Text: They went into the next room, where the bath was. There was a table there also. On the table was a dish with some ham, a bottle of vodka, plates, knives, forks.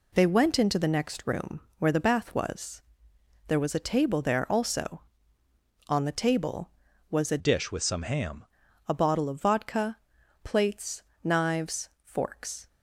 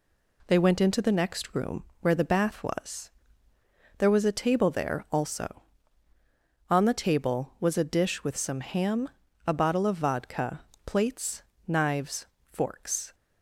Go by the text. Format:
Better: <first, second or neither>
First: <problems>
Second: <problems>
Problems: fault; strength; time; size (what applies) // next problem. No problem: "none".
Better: second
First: changes voice from "dish" to "ham"; from 7.3 to 8.4 s; 1.1 s long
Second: none